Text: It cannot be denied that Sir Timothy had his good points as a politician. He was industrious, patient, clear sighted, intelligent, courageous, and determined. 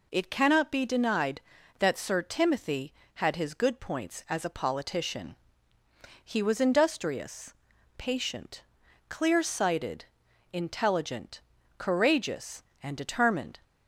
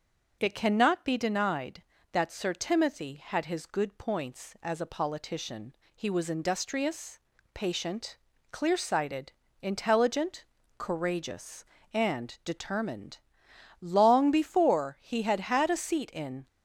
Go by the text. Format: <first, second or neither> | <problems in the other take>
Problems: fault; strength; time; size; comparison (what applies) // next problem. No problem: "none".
first | goes on to say "Long before he had had a seat in"; strong; from 13.8 s on; 2.6 s long